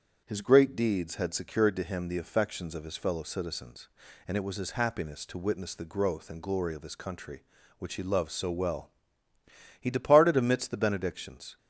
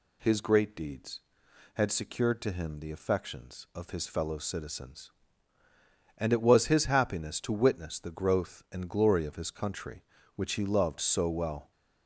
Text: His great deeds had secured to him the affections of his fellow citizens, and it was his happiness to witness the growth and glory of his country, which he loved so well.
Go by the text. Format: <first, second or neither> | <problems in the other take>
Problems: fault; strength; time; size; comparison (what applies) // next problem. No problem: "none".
second | starts louder than the rest; strong; until 1.2 s; 7 dB // goes on to say "He departed amidst the benedictions"; strong; from 9.8 s on; 1.7 s long